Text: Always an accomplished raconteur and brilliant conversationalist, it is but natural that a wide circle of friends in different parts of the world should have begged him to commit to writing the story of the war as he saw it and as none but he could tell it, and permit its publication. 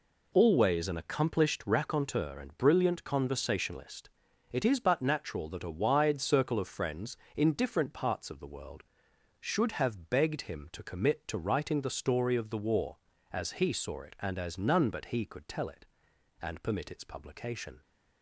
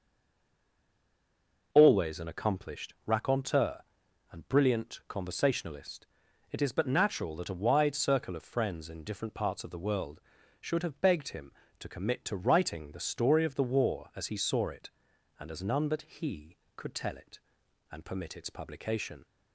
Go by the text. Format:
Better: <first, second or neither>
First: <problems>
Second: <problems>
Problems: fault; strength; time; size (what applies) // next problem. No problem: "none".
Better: first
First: none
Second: stays silent before the first word; noticeable; until 1.7 s; 1.7 s long